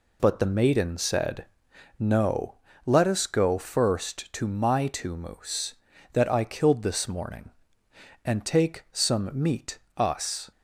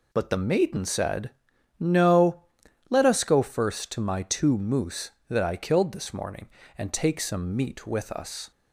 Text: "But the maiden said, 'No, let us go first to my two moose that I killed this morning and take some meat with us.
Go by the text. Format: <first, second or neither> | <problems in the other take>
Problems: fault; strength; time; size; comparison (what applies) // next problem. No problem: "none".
second | skips "with"; at 9.8 s